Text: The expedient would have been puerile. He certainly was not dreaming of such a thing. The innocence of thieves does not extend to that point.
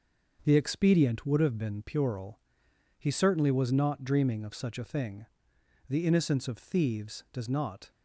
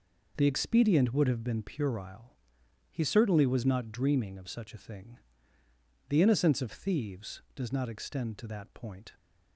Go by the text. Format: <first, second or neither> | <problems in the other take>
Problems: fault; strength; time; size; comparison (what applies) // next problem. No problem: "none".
second | starts louder than the rest; until 1.4 s; 6 dB // stops before "extend to that point"; at 7.9 s